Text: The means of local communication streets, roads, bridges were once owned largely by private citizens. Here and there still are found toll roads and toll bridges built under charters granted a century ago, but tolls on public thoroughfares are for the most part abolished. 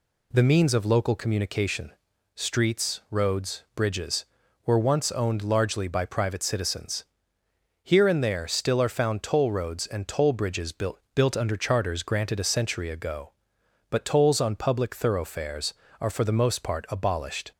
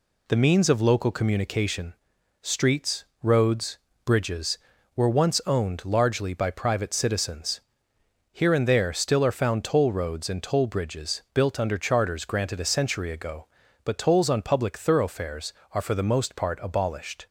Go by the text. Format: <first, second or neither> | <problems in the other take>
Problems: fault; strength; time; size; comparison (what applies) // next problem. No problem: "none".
second | pauses between "communication" and "streets"; at 1.9 s; 0.44 s long; noticeable in the second // says "built" twice; at 11.1 s